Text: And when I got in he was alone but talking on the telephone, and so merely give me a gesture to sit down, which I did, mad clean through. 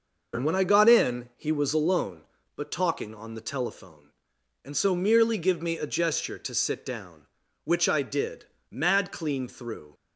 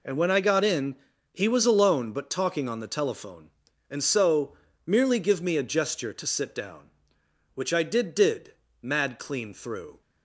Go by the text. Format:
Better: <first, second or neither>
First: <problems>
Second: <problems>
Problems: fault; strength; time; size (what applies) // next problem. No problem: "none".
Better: first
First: none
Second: pauses between "in" and "he"; at 0.9 s; 0.38 s long // pauses between "so" and "merely"; slight; at 4.5 s; 0.28 s long // says "did" twice; at 8.1 s